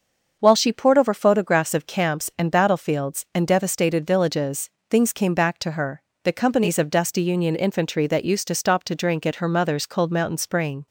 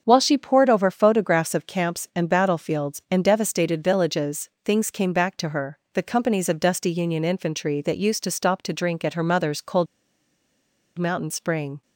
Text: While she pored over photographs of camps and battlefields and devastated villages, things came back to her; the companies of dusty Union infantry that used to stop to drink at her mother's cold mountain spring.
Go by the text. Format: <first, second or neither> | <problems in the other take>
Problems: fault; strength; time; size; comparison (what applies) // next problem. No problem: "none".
first | starts louder than the rest; until 1.0 s; 7 dB; also in the first // pauses between "cold" and "mountain"; at 9.8 s; 1.1 s long